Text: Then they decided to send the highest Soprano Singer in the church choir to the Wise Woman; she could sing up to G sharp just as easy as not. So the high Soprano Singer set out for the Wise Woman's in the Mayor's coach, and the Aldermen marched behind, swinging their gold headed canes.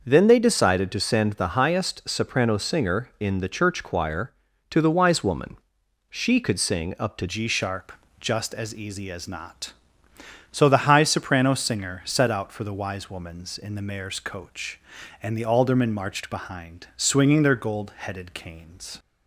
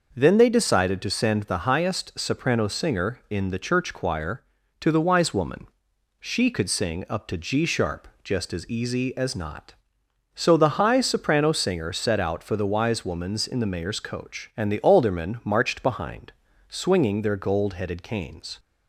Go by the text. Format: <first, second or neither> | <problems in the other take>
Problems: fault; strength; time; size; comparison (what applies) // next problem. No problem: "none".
second | starts louder than the rest; until 1.0 s; 6 dB // changes voice at "G"; from 7.2 s on; 11.7 s long // pauses between "sharp" and "just"; slight; at 7.9 s; 0.26 s long